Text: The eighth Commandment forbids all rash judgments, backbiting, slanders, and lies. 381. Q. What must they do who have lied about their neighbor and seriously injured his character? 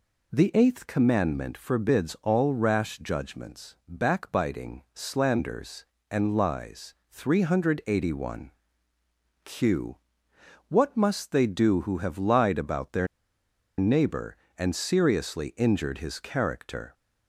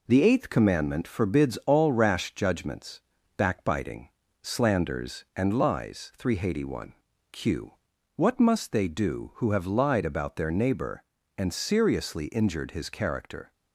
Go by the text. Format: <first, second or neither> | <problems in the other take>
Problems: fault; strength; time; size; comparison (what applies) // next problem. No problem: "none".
second | pauses between "their" and "neighbor"; noticeable; at 13.0 s; 0.72 s long